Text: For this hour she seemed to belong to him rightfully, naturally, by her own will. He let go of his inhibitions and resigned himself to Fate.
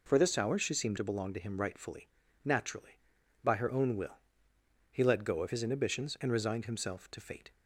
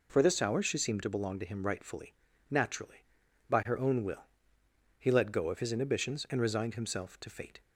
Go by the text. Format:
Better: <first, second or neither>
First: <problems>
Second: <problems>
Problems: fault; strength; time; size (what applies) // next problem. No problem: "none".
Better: neither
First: none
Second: none